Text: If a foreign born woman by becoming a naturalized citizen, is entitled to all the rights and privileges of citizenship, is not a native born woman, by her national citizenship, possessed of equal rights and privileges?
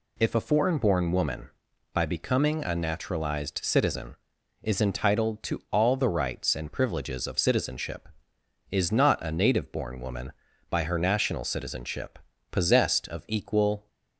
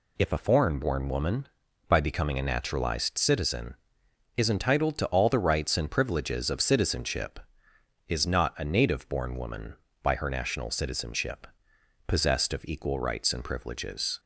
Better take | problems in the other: second | stops before "rights and privileges"; at 13.8 s

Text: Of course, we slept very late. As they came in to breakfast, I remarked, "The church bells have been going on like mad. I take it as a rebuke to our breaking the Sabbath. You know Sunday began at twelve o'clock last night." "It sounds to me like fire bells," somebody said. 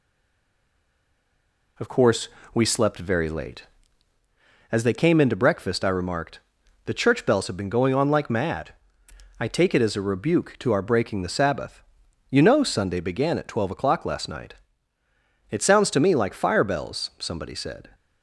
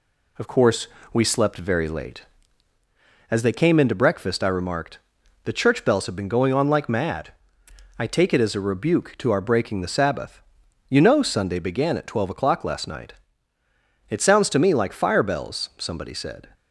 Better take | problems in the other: second | stays silent before the first word; noticeable; until 1.7 s; 1.7 s long

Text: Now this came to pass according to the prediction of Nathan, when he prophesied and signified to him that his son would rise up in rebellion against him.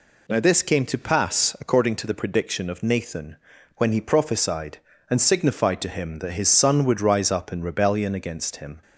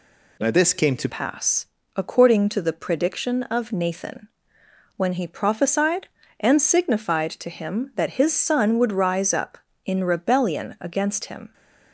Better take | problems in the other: first | changes voice at "pass"; from 1.0 s on; 10.5 s long // pauses between "pass" and "according"; slight; at 1.6 s; 0.28 s long

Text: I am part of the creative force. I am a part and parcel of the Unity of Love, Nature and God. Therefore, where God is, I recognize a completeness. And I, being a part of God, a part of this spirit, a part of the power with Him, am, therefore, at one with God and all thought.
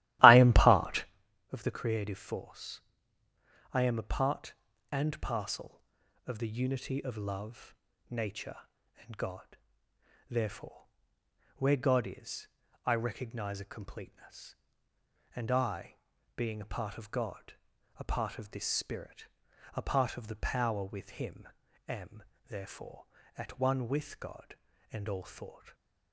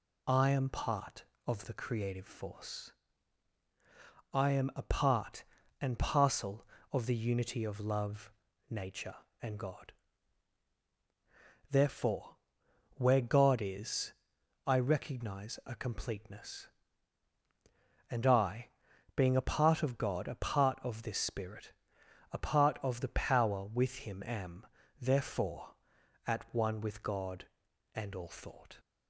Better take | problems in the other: second | starts louder than the rest; strong; until 1.2 s; 15.5 dB

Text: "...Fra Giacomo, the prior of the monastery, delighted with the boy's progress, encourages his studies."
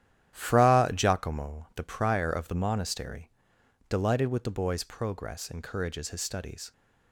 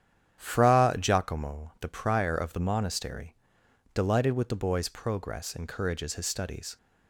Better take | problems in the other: second | gets quieter; strong; throughout; 9.5 dB // starts louder than the rest; strong; until 1.3 s; 11 dB; strong in the second

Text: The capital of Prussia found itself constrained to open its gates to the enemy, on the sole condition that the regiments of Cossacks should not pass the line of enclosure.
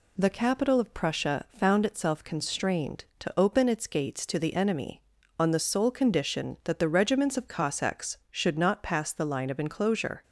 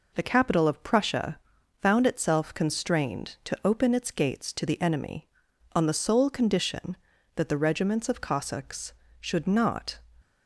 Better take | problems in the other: first | pauses between "Prussia" and "found"; at 1.3 s; 0.42 s long // stops before "pass the line of enclosure"; at 10.2 s

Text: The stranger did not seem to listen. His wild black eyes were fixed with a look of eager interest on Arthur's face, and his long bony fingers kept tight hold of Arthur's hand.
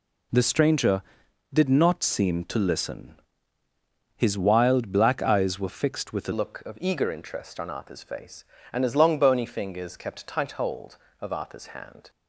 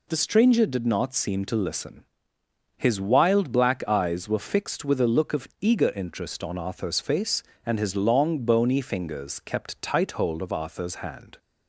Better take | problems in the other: second | changes voice at "look"; from 6.3 s on; 5.7 s long

